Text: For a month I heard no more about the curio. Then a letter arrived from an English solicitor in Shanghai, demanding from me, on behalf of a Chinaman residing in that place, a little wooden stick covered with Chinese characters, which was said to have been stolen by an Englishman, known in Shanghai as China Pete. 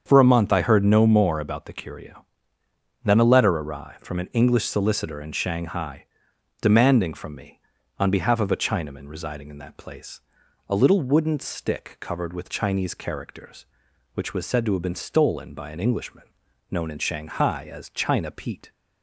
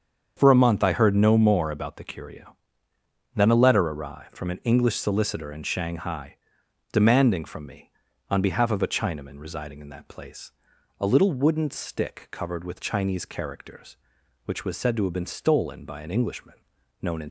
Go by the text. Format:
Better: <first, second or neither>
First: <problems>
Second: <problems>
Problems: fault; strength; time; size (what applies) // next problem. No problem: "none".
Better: first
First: starts louder than the rest; strong; until 1.0 s; 7.5 dB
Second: starts louder than the rest; strong; until 1.3 s; 7.5 dB // stops before "Shanghai as China Pete"; at 17.2 s